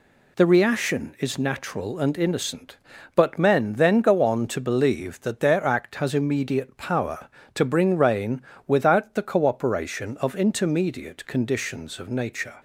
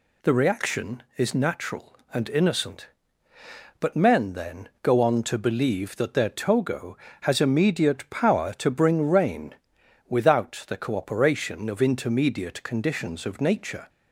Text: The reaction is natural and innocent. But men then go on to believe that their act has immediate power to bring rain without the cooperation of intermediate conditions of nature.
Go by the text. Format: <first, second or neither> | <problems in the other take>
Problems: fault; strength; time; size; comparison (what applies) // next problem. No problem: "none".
first | pauses between "then" and "go"; slight; at 4.6 s; 0.16 s long // says "togo" for "act"; at 6.2 s // pauses between "rain" and "without"; noticeable; at 9.5 s; 0.54 s long; slight in the first